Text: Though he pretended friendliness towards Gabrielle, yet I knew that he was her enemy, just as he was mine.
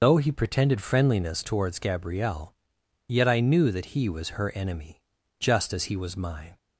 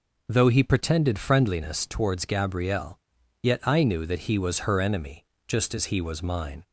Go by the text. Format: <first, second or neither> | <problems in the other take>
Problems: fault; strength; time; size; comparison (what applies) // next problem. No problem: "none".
second | loses the start of "Though"; at 0.0 s; 90 ms